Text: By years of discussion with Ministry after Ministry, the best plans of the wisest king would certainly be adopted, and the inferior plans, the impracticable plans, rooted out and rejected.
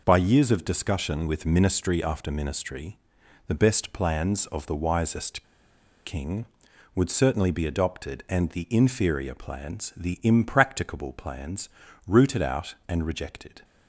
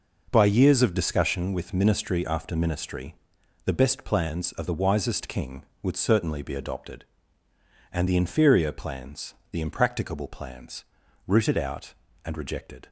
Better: second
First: pauses between "wisest" and "king"; noticeable; at 5.4 s; 0.62 s long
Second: none

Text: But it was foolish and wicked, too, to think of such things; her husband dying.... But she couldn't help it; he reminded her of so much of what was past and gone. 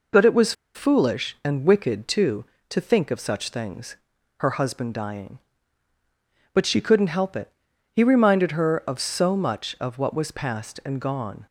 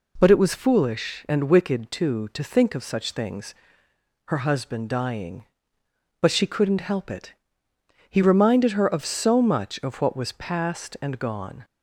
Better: second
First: pauses between "was" and "foolish"; slight; at 0.5 s; 0.22 s long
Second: none

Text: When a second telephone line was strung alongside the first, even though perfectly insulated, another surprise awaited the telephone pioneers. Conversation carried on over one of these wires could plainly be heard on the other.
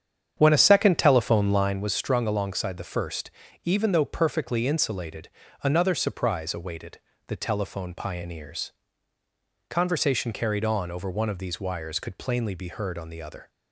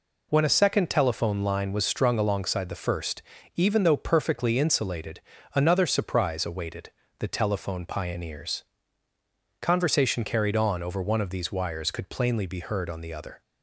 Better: second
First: starts louder than the rest; strong; until 1.9 s; 8.5 dB // pauses between "awaited" and "the"; slight; at 6.9 s; 0.26 s long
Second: pauses between "awaited" and "the"; slight; at 6.9 s; 0.26 s long

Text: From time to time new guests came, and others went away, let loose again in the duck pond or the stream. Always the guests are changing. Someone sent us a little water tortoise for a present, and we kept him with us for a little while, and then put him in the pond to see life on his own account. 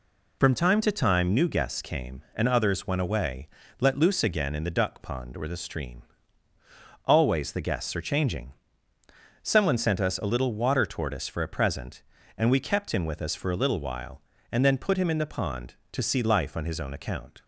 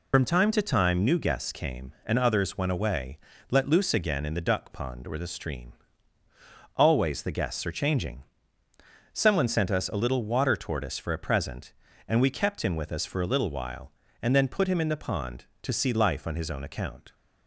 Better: first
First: none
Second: loses the start of "From"; at 0.1 s; 30 ms

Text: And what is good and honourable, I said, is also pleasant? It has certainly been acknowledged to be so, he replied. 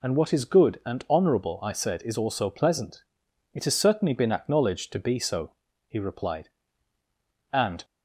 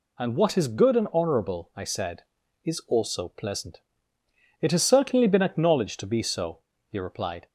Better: second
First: goes on to say "And"; slight; from 7.5 s on; 0.32 s long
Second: none

